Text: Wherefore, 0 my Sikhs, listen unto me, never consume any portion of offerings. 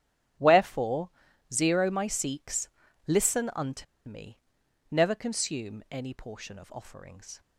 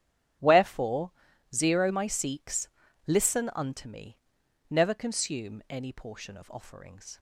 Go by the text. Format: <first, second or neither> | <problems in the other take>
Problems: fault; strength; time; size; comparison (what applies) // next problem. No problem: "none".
second | starts louder than the rest; strong; until 1.8 s; 13.5 dB; strong in the second // pauses between "unto" and "me"; slight; at 3.8 s; 0.23 s long